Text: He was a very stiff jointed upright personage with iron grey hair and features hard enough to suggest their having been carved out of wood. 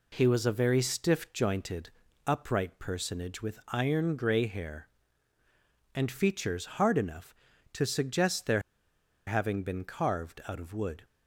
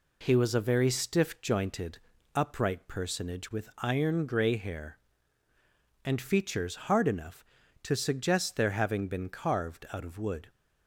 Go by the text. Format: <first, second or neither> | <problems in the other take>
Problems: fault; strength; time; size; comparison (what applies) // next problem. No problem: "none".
second | pauses between "jointed" and "upright"; at 1.8 s; 0.38 s long; also in the second // pauses between "their" and "having"; noticeable; at 8.6 s; 0.65 s long